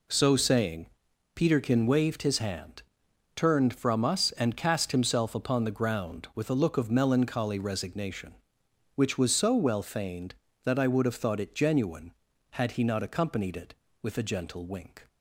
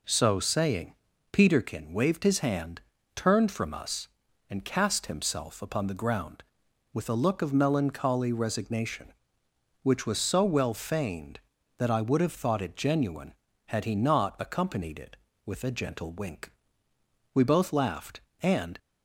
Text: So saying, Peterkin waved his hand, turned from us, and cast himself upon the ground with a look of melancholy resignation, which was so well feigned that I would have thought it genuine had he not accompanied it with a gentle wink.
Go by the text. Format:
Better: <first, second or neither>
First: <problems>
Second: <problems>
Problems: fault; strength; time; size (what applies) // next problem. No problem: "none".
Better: first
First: none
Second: goes on to say "We both laughed and"; from 17.3 s on; 1.4 s long